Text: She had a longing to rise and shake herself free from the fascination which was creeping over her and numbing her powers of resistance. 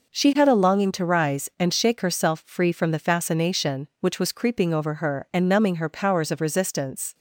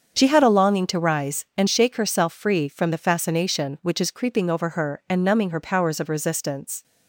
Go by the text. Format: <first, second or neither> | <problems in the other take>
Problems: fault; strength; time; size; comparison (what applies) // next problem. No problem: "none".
first | starts louder than the rest; until 1.1 s; 7 dB // says "is" for "was"; at 4.0 s